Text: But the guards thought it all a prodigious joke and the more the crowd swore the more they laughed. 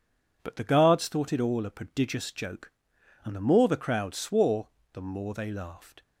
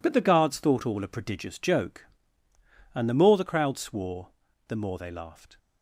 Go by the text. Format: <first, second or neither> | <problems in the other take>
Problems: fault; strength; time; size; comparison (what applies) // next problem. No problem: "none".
first | skips "it"; at 0.8 s // pauses between "swore" and "the"; at 4.2 s; 0.38 s long; slight in the first